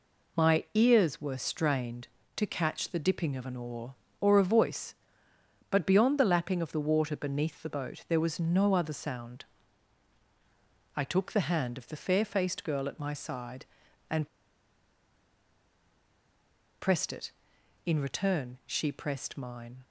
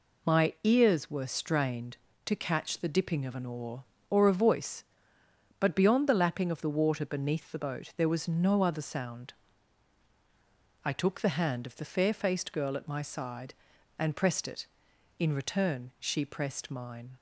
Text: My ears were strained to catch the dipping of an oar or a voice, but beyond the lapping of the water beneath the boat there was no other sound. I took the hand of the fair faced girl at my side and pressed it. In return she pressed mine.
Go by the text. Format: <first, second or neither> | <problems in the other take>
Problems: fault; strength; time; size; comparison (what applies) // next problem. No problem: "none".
second | pauses between "and" and "pressed"; strong; at 14.2 s; 2.5 s long